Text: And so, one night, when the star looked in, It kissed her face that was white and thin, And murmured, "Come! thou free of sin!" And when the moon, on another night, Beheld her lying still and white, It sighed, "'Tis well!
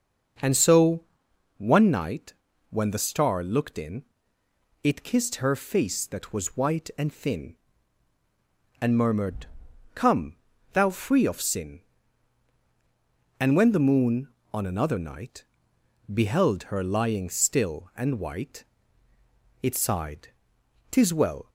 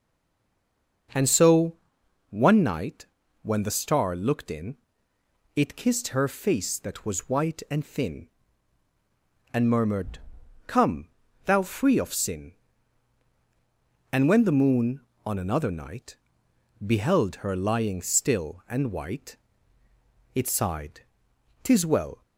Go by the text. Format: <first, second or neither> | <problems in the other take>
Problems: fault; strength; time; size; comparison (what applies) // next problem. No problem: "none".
first | stays silent before the first word; until 1.0 s; 1.0 s long